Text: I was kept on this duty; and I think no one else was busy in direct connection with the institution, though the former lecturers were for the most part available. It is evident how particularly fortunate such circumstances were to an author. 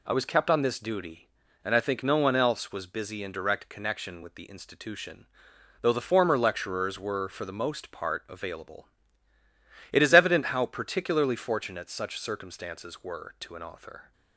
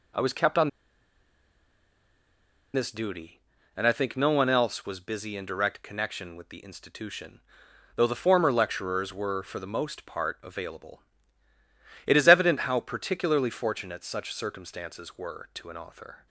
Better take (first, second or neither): first